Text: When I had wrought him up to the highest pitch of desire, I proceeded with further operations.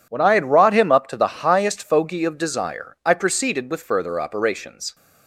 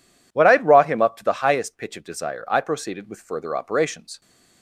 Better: second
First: says "fogey" for "pitch"; at 1.8 s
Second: none

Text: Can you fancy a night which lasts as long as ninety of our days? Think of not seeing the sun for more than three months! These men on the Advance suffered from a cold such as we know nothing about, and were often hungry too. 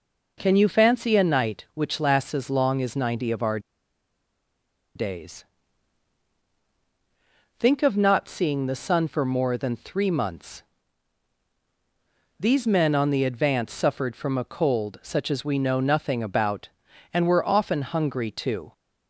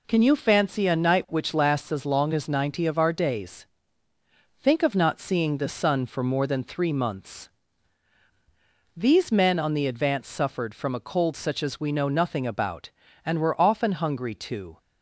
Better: second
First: pauses between "our" and "days"; strong; at 3.5 s; 1.3 s long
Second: none

